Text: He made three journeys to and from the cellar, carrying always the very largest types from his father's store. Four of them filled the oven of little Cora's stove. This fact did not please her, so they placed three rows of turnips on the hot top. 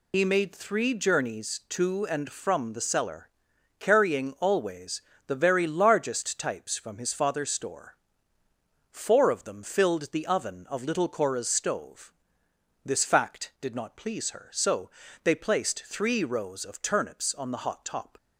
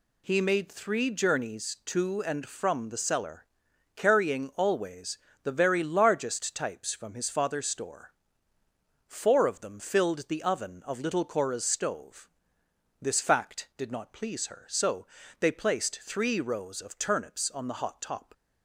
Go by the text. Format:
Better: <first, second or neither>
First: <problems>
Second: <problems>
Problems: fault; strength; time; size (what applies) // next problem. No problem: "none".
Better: second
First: loses the start of "He"; at 0.1 s; 55 ms // pauses between "always" and "the"; slight; at 5.0 s; 0.24 s long // pauses between "so" and "they"; slight; at 14.8 s; 0.36 s long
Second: pauses between "always" and "the"; slight; at 5.1 s; 0.24 s long // pauses between "so" and "they"; slight; at 15.0 s; 0.36 s long